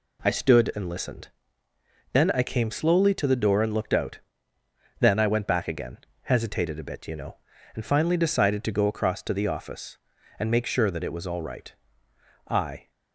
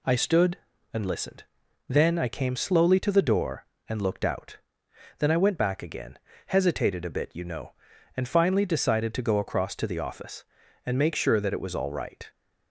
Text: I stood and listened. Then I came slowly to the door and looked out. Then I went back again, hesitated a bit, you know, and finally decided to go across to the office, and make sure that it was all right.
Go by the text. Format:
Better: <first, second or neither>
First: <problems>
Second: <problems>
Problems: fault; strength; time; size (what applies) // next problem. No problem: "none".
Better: second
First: goes on to say "I"; slight; from 12.4 s on; 0.42 s long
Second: none